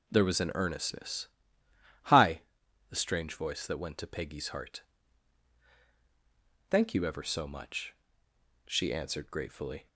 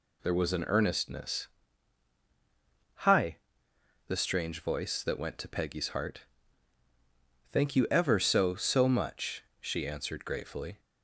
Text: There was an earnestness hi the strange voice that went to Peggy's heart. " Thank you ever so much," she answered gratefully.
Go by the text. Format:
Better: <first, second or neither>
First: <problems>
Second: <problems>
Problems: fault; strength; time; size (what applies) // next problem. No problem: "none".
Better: first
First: pauses between "earnestness" and "hi"; noticeable; at 1.2 s; 0.76 s long // pauses between "hi" and "the"; noticeable; at 2.3 s; 0.50 s long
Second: pauses between "earnestness" and "hi"; strong; at 1.4 s; 1.5 s long // pauses between "hi" and "the"; noticeable; at 3.3 s; 0.70 s long // says "so" twice; at 8.5 s